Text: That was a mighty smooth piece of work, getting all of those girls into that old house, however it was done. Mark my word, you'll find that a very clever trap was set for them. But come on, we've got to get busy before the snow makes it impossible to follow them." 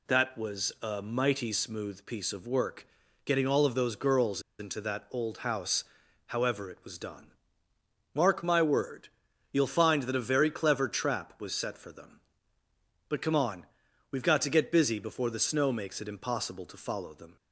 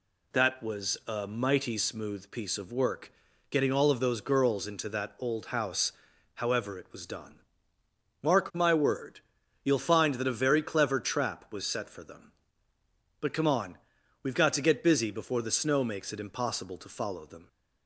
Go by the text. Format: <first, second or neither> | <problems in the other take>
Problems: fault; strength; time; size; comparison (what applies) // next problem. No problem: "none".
second | pauses between "girls" and "into"; slight; at 4.4 s; 0.18 s long